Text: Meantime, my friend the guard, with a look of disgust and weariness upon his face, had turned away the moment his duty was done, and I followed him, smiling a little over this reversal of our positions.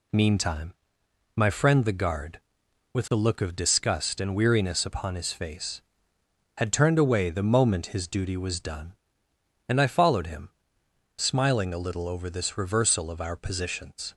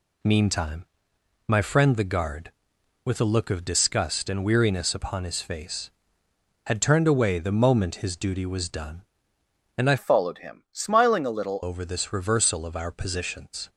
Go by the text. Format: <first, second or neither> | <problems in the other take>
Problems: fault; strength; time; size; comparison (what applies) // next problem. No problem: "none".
first | changes voice from "followed" to "little"; from 9.9 to 11.6 s; 1.7 s long